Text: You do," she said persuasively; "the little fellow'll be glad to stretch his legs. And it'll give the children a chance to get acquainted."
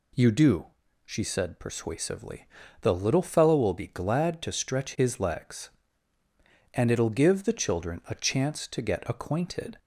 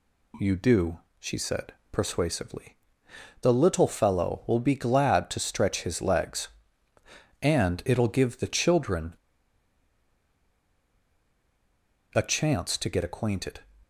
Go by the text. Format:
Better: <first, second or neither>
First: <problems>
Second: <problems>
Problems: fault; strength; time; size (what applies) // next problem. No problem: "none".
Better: first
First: none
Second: pauses between "said" and "persuasively"; slight; at 1.7 s; 0.22 s long // pauses between "children" and "a"; strong; at 9.1 s; 3.0 s long